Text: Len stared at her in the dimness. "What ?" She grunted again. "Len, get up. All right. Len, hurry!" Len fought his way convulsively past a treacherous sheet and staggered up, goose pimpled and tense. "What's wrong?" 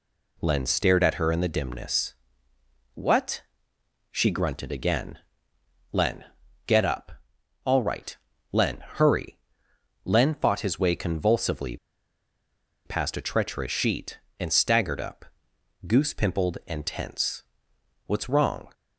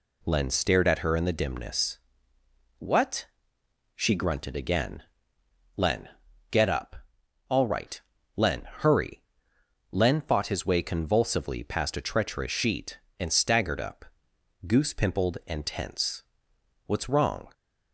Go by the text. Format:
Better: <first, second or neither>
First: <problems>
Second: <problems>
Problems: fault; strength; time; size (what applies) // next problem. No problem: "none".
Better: second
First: pauses between "convulsively" and "past"; at 11.7 s; 1.0 s long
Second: none